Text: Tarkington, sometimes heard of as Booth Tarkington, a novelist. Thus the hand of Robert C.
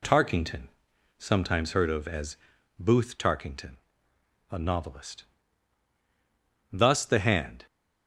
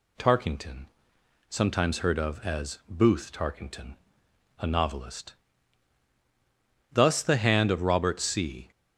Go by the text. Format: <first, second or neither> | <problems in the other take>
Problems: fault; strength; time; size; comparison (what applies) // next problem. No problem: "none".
second | pauses between "as" and "Booth"; at 2.3 s; 0.44 s long // stops before "of Robert C"; at 7.6 s